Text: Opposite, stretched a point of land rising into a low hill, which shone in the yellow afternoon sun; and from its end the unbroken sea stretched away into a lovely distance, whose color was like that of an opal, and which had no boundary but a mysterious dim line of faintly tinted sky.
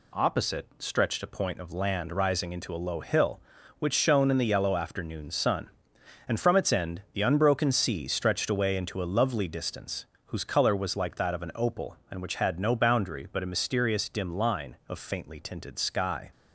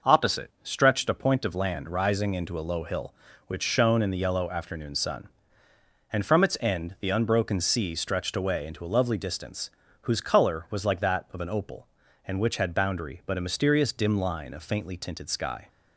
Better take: first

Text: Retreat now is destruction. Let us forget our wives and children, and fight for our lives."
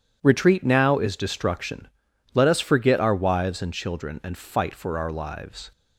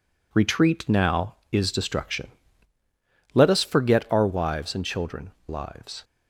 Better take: first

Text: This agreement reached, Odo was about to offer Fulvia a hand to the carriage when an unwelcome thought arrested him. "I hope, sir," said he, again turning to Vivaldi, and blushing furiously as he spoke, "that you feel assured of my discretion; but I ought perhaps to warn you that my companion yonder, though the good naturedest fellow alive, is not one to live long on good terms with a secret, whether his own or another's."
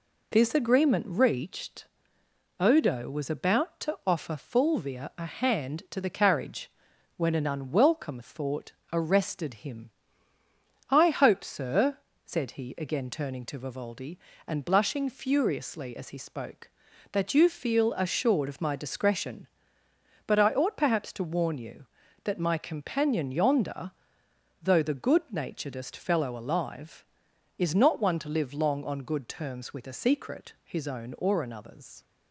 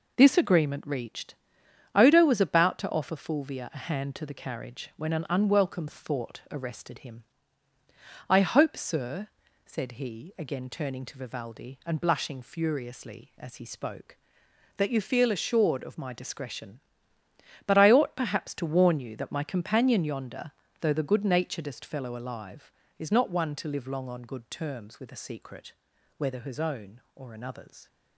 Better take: second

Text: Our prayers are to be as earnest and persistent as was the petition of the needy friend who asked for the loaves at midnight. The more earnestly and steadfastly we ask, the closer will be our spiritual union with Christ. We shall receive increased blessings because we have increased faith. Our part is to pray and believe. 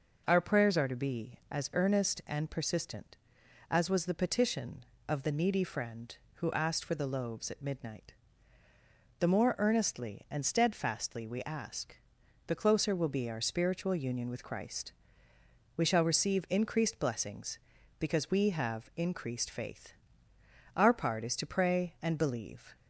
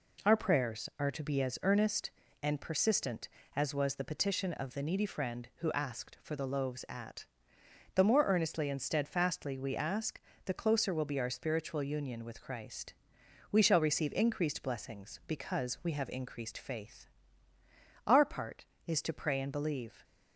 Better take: first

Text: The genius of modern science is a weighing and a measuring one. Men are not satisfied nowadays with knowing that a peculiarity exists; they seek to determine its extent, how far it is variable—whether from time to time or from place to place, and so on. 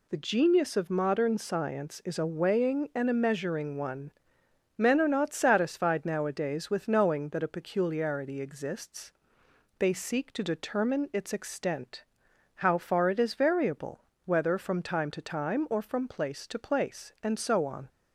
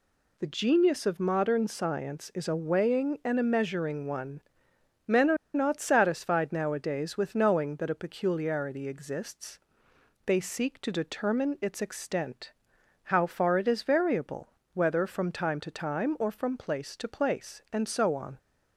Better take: first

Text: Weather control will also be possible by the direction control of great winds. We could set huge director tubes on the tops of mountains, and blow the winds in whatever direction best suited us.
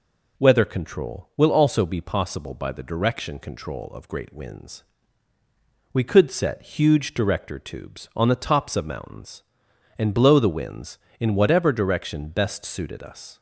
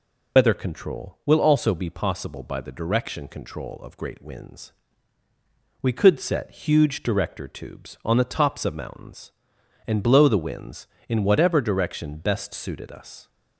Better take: first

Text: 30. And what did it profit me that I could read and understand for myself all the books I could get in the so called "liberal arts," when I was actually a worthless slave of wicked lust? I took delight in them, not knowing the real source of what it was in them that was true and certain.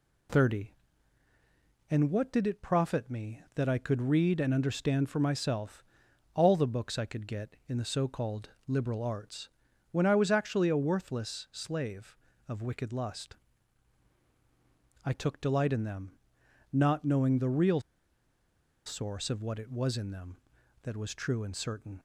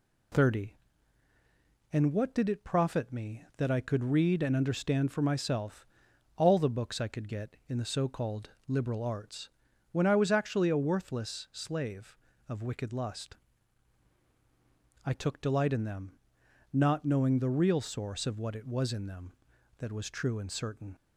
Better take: second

